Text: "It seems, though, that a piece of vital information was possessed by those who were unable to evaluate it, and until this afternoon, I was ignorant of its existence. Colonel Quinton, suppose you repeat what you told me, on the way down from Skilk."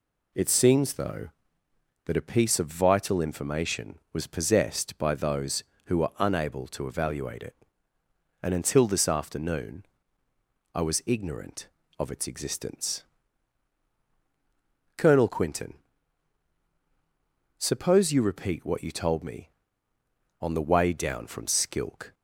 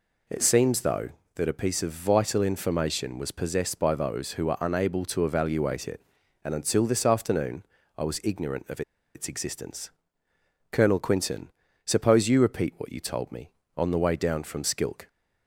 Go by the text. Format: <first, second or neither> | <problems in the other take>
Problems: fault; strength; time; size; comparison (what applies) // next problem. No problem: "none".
first | pauses between "of" and "its"; slight; at 8.8 s; 0.33 s long